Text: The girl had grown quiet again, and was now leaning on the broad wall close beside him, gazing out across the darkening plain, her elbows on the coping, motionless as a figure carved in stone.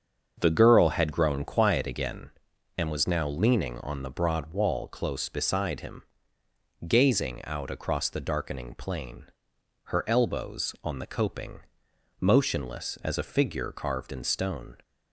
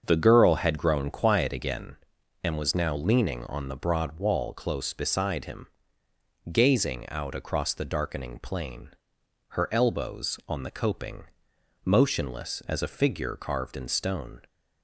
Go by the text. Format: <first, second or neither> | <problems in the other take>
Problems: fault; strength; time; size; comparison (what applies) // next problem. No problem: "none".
neither | starts louder than the rest; the same in both